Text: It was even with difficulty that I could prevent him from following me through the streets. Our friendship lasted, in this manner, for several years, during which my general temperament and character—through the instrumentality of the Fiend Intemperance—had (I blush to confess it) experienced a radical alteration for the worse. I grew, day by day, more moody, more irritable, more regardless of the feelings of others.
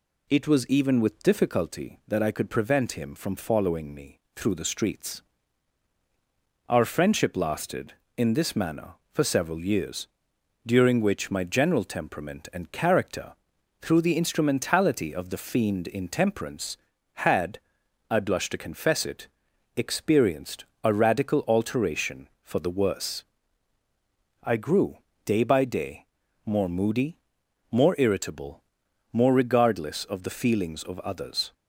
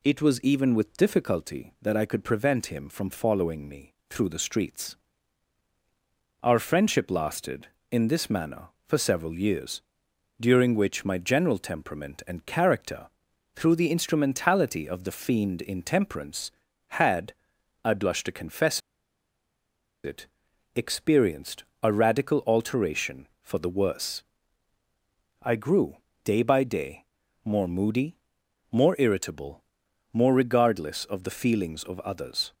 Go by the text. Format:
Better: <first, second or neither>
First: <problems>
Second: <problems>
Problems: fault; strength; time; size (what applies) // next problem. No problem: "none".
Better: first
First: pauses between "me" and "through"; slight; at 4.1 s; 0.16 s long // pauses between "experienced" and "a"; slight; at 20.6 s; 0.18 s long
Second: pauses between "me" and "through"; slight; at 3.9 s; 0.16 s long // pauses between "confess" and "it"; strong; at 18.8 s; 1.2 s long // pauses between "experienced" and "a"; slight; at 21.6 s; 0.18 s long